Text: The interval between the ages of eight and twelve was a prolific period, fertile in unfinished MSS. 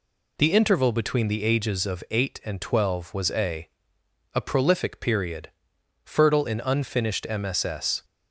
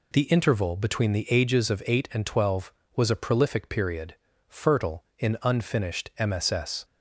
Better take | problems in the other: second | says "a" twice; at 4.3 s

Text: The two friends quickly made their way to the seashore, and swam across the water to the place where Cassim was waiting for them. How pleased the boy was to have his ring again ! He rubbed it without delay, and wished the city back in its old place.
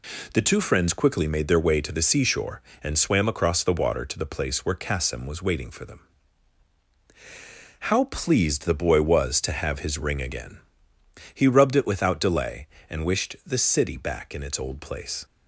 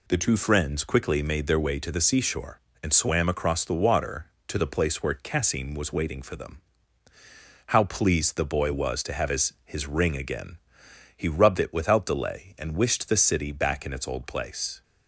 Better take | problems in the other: first | says "his" twice; at 9.6 s

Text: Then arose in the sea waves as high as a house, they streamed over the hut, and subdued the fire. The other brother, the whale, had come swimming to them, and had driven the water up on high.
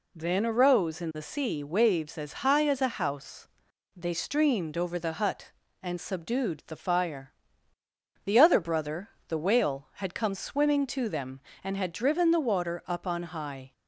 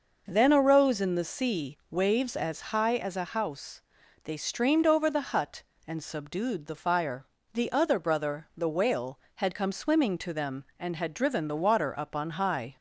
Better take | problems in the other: neither | none

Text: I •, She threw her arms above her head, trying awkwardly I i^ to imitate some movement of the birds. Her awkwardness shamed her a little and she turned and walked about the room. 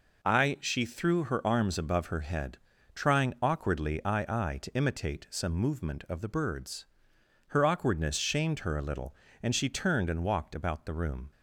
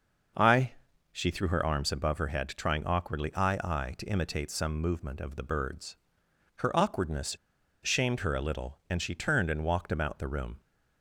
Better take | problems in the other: first | pauses between "awkwardness" and "shamed"; noticeable; at 7.3 s; 0.47 s long

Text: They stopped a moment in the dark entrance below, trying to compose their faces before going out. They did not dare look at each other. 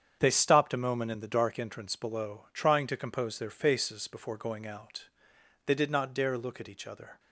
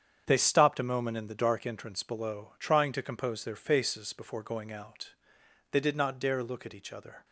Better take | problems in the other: neither | starts louder than the rest; strong; the same in both

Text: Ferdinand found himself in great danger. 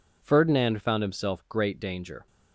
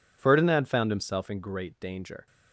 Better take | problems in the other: second | skips "in"; at 1.4 s

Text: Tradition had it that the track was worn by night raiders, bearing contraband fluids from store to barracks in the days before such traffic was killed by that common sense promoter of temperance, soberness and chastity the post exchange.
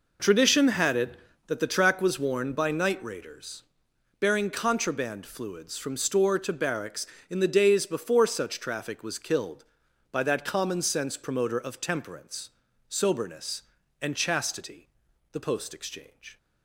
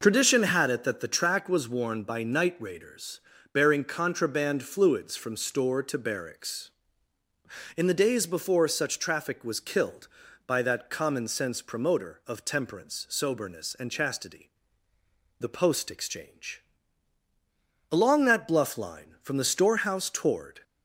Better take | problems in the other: first | pauses between "chastity" and "the"; noticeable; at 14.4 s; 0.88 s long; also in the first // goes on to say "Along that bluff line from the storehouse toward"; strong; from 17.9 s on; 2.7 s long

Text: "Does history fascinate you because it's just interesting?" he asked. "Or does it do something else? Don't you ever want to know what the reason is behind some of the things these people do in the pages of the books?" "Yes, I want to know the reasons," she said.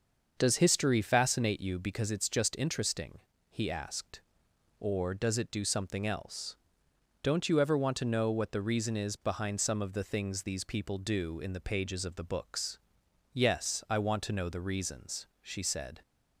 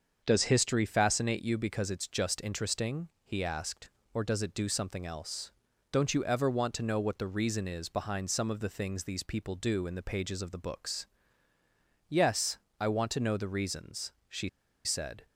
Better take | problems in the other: first | starts louder than the rest; until 1.2 s; 6.5 dB; also in the first // pauses between "she" and "said"; at 14.4 s; 0.36 s long

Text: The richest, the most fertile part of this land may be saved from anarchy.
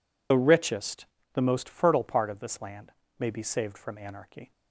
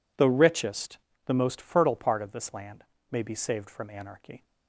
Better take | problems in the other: second | loses the start of "The"; at 0.3 s; 65 ms // pauses between "land" and "may"; slight; at 2.9 s; 0.26 s long; slight in the second

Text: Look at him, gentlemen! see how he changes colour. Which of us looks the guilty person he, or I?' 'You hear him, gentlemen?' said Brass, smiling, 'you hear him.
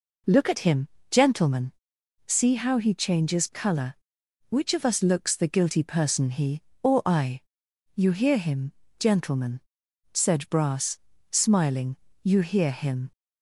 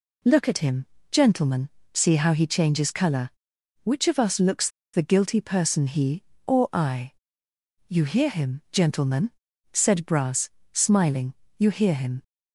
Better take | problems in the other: first | pauses between "looks" and "the"; slight; at 4.6 s; 0.25 s long

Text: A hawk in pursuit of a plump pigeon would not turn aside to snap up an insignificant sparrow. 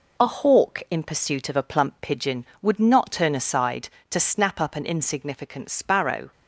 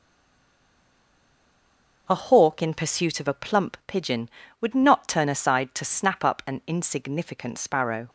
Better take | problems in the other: first | stays silent before the first word; noticeable; until 2.0 s; 2.0 s long

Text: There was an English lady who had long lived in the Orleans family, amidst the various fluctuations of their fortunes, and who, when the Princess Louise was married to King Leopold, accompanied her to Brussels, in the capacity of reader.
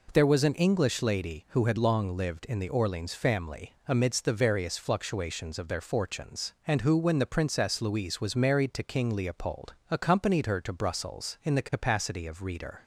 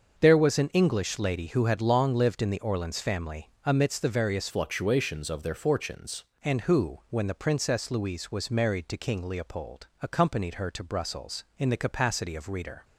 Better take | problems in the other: first | starts louder than the rest; until 1.1 s; 6.5 dB // changes voice from "fluctuations" to "fortunes"; from 4.4 to 6.2 s; 1.8 s long

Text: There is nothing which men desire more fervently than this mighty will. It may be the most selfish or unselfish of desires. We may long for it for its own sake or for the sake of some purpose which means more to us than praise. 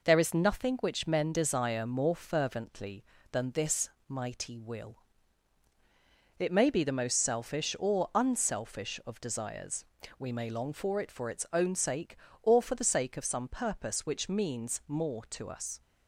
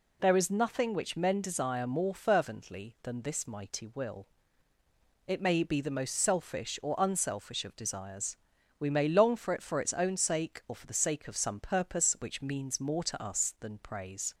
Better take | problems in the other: second | pauses between "this" and "mighty"; slight; at 3.8 s; 0.18 s long // stops before "than praise"; at 15.8 s

